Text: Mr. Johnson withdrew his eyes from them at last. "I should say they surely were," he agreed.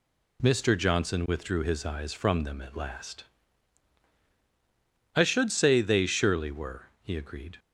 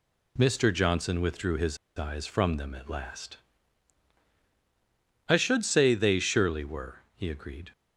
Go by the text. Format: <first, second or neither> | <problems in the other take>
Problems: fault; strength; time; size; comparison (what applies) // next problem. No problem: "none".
first | pauses between "his" and "eyes"; slight; at 1.7 s; 0.20 s long